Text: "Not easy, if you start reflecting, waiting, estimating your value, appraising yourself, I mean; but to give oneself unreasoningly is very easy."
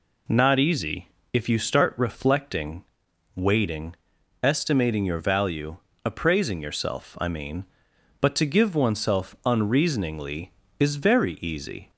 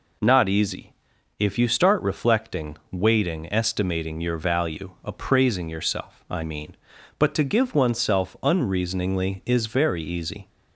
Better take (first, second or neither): neither